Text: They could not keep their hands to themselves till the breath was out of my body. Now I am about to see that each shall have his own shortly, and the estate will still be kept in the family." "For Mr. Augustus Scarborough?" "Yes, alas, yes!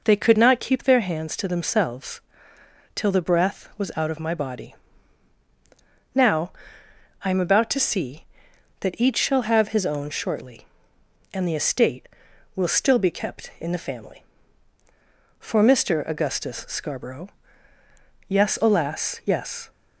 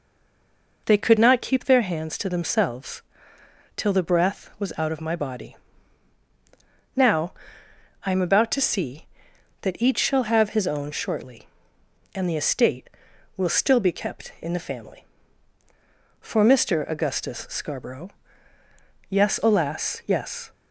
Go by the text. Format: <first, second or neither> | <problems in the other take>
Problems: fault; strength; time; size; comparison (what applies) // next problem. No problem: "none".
first | stays silent before the first word; slight; until 0.8 s; 0.8 s long // pauses between "themselves" and "till"; noticeable; at 3.0 s; 0.74 s long; noticeable in the first // pauses between "Now" and "I"; noticeable; at 7.3 s; 0.72 s long; noticeable in the first